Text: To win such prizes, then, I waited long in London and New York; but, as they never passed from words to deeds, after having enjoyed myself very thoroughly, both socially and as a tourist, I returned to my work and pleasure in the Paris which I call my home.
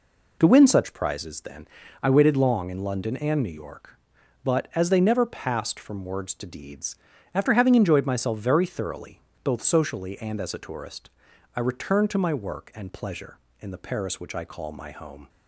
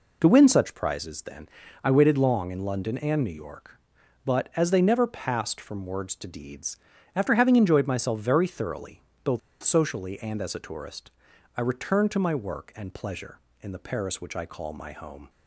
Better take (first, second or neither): first